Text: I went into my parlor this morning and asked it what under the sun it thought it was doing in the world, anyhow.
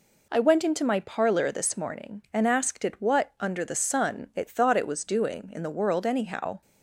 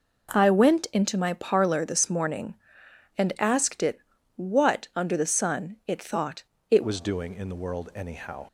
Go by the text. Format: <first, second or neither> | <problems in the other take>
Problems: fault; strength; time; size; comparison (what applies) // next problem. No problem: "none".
first | pauses between "it" and "what"; at 3.9 s; 0.38 s long // pauses between "thought" and "it"; slight; at 6.4 s; 0.26 s long // changes voice at "was"; from 6.8 s on; 1.6 s long